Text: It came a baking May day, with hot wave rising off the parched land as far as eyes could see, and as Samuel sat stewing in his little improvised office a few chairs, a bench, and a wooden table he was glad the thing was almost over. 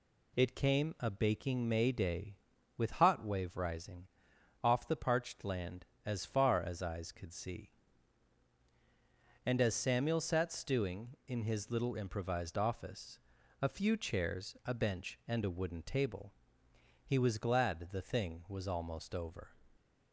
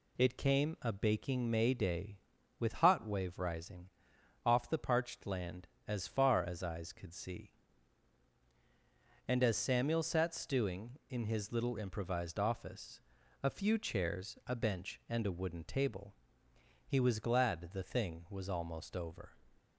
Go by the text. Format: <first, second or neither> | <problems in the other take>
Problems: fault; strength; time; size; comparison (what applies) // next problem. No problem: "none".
neither | pauses between "rising" and "off"; noticeable; the same in both // pauses between "office" and "a"; the same in both // pauses between "table" and "he"; noticeable; the same in both